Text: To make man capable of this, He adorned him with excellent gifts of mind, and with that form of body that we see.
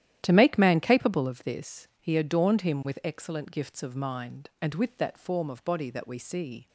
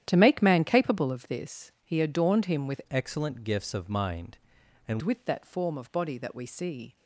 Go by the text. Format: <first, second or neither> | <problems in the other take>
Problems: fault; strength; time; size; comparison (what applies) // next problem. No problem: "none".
first | starts louder than the rest; strong; until 1.0 s; 11 dB; strong in the first // changes voice from "excellent" to "and"; from 2.8 to 4.9 s; 2.1 s long